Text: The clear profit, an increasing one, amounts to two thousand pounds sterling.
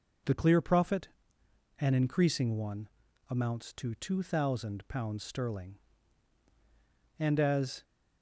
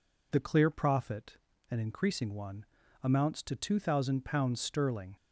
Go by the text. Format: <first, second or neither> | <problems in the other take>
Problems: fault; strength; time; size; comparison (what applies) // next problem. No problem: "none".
second | goes on to say "And as"; noticeable; from 7.1 s on; 0.64 s long